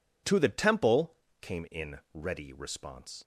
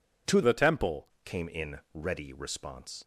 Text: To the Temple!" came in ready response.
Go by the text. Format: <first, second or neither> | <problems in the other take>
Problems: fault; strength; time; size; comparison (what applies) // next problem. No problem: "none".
first | changes voice from "the" to "Temple"; from 0.4 to 1.0 s; 0.6 s long